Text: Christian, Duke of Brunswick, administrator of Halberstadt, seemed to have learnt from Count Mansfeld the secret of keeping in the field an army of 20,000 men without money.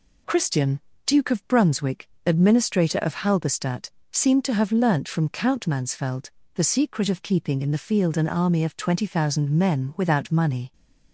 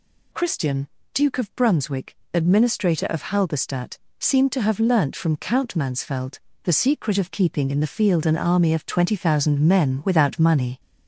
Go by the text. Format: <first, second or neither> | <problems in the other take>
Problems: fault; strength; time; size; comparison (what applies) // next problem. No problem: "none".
first | gets louder; slight; throughout; 2.5 dB // pauses between "Mansfeld" and "the"; slight; at 6.3 s; 0.24 s long; slight in the first